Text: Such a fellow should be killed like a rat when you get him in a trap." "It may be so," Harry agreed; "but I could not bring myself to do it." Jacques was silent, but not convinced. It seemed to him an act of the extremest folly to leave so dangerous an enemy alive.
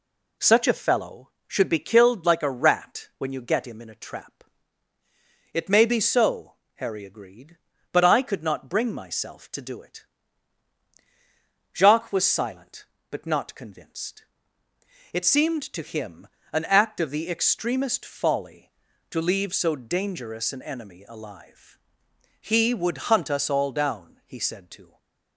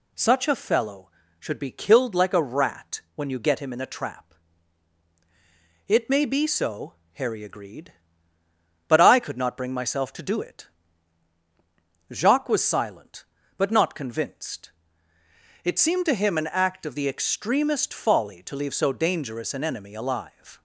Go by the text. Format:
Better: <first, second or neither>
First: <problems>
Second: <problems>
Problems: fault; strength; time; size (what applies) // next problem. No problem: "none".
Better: second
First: pauses between "him" and "an"; slight; at 16.2 s; 0.24 s long // goes on to say "He would hunt us all down he said to"; strong; from 22.3 s on; 2.5 s long // stays silent after the last word; slight; from 24.8 s on; 0.5 s long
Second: none